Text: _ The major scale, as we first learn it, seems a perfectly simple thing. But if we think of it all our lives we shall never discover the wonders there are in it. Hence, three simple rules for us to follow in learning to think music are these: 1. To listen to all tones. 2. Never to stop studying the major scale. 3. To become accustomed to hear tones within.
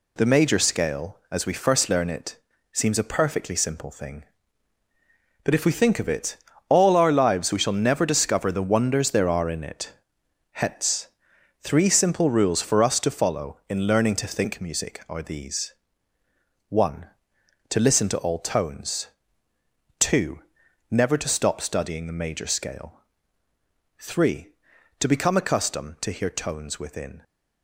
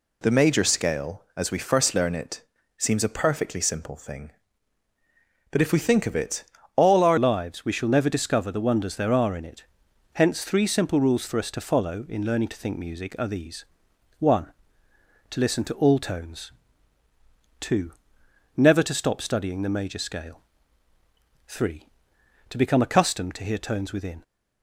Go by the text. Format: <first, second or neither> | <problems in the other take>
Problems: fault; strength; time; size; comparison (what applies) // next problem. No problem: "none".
first | pauses between "it" and "all"; slight; at 6.4 s; 0.30 s long; slight in the first // changes voice at "lives"; from 7.1 s on; 17.1 s long